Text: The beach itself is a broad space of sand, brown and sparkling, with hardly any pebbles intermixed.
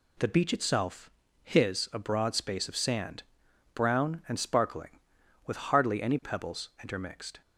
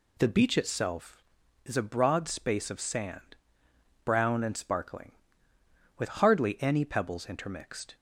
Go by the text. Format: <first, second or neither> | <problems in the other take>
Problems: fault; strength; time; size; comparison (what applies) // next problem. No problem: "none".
second | says "his" for "is"; at 1.4 s